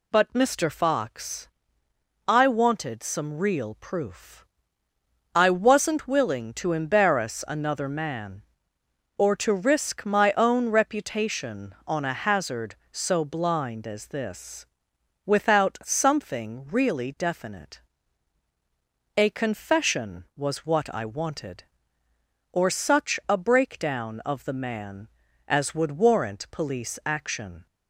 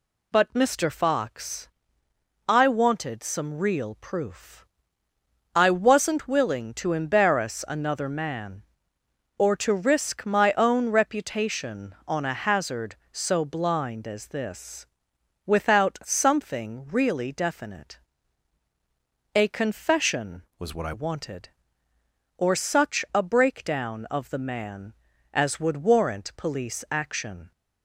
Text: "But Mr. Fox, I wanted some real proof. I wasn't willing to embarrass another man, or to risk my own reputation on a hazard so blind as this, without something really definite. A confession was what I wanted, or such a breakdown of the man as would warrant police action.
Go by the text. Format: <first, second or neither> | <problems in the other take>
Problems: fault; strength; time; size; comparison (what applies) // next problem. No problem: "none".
first | changes voice from "was" to "I"; from 20.5 to 20.9 s; 0.4 s long